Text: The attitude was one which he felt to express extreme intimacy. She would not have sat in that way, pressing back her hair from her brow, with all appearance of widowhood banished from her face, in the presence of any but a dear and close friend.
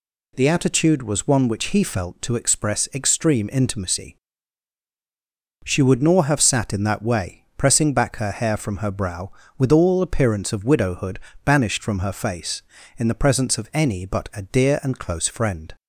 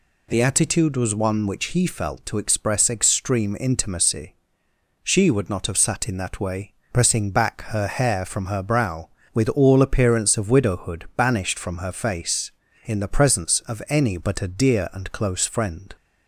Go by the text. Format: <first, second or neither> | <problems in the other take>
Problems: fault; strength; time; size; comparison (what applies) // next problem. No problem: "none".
second | says "nor" for "not"; at 6.0 s // pauses between "widowhood" and "banished"; slight; at 11.2 s; 0.24 s long